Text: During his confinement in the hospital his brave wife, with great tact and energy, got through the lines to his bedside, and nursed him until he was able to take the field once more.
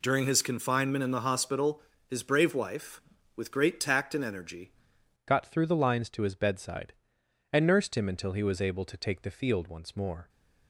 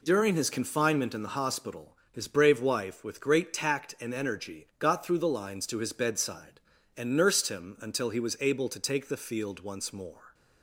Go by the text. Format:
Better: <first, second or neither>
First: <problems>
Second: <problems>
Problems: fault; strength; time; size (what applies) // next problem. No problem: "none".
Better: second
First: pauses between "hospital" and "his"; slight; at 1.8 s; 0.26 s long // changes voice at "got"; from 5.2 s on; 5.0 s long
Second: none